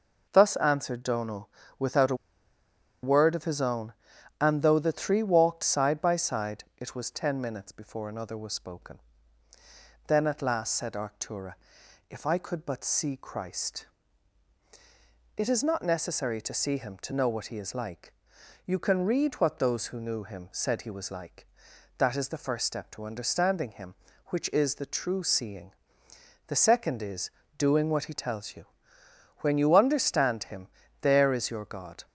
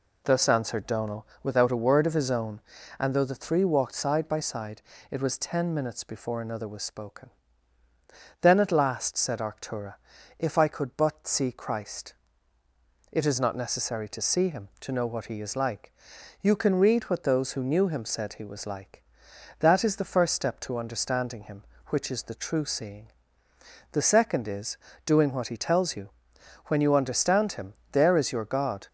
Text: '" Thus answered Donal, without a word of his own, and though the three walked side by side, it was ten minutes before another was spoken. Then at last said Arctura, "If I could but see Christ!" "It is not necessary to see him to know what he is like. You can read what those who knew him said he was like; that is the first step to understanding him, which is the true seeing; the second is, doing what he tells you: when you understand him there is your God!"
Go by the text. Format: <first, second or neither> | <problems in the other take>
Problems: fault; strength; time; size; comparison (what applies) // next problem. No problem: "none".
second | pauses between "a" and "word"; noticeable; at 2.1 s; 0.87 s long // pauses between "him" and "there"; slight; at 30.6 s; 0.34 s long; slight in the second